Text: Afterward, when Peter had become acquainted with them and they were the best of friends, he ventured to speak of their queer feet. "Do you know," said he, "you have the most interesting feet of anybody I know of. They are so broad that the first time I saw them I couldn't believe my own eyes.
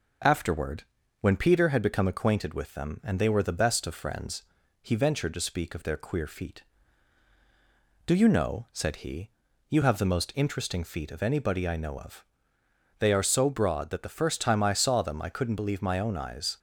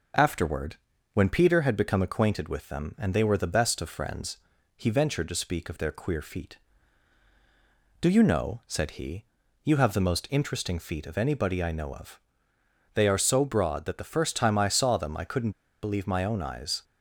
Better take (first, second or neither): first